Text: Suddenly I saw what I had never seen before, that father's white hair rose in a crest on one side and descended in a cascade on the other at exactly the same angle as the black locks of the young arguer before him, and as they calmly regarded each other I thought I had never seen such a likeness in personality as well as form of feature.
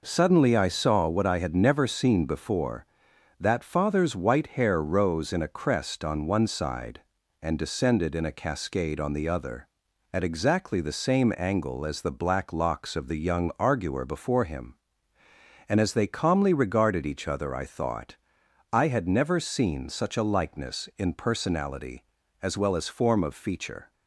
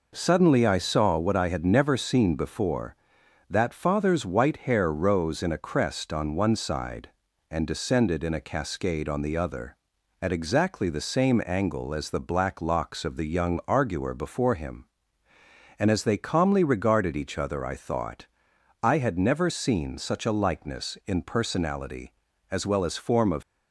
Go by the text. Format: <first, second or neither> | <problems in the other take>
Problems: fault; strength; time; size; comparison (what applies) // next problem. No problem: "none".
first | pauses between "thought" and "I"; noticeable; at 18.2 s; 0.56 s long; noticeable in the first // stops before "feature"; at 23.4 s